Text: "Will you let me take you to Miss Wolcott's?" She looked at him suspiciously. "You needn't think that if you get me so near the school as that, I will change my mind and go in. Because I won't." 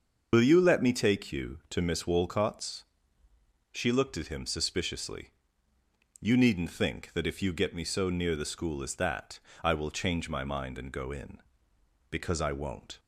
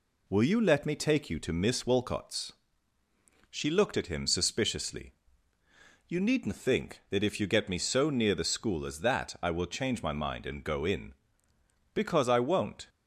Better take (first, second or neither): second